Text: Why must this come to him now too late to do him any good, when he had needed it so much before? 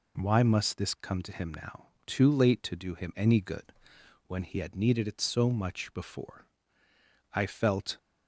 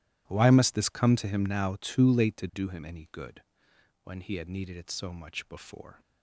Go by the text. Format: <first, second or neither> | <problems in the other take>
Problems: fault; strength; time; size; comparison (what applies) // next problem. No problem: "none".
second | pauses between "now" and "too"; slight; at 1.8 s; 0.18 s long // goes on to say "I felt"; noticeable; from 7.3 s on; 0.64 s long